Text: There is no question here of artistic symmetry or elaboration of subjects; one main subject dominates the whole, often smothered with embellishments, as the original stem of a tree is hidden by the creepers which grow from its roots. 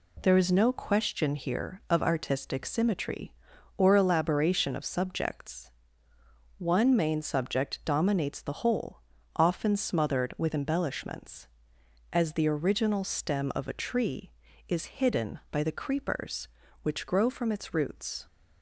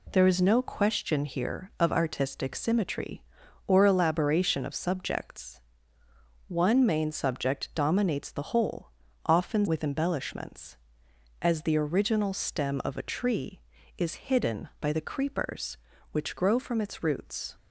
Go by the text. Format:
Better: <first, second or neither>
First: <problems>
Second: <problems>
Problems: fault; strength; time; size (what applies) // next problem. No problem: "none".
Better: first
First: none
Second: skips "smothered"; at 9.6 s